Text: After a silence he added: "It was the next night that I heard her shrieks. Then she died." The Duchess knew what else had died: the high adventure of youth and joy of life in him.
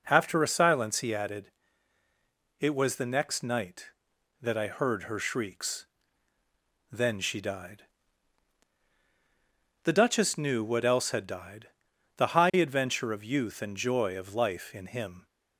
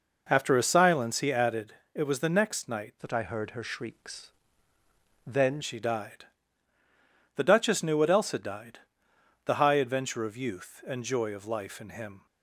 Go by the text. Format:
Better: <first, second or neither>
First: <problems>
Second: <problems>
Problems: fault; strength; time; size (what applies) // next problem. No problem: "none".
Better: first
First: none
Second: changes voice from "that" to "Then"; from 3.0 to 5.5 s; 2.5 s long